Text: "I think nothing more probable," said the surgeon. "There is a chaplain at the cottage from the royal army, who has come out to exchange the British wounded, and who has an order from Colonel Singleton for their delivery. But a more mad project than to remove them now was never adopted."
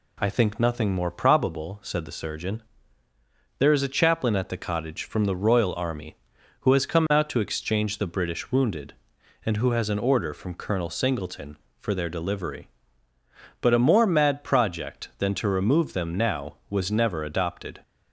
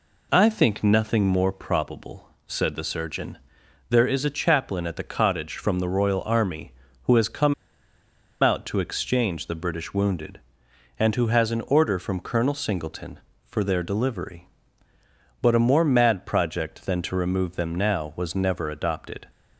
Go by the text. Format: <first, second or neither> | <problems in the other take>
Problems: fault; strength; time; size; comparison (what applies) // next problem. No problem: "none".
first | pauses between "come" and "out"; noticeable; at 7.5 s; 0.88 s long